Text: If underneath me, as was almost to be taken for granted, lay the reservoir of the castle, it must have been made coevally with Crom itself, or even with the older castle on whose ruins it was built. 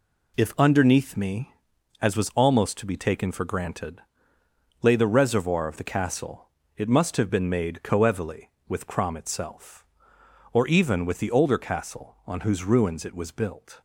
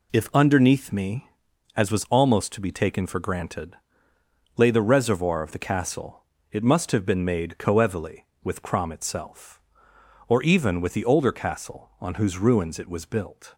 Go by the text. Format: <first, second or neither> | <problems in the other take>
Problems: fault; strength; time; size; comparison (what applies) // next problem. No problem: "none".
neither | none